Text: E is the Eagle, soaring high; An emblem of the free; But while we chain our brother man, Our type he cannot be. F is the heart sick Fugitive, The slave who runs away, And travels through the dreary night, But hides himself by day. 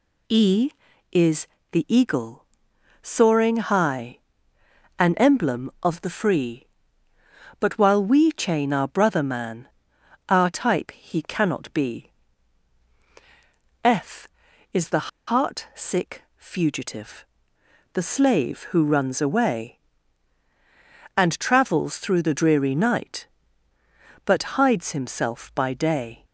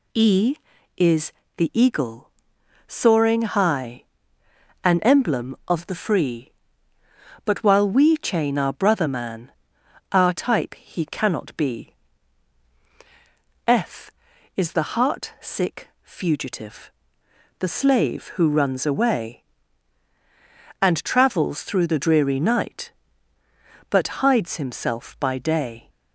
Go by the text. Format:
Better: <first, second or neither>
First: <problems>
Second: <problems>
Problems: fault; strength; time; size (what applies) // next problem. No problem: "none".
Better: second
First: pauses between "is" and "the"; slight; at 1.4 s; 0.24 s long // pauses between "the" and "heart"; slight; at 15.0 s; 0.20 s long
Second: pauses between "is" and "the"; slight; at 1.3 s; 0.24 s long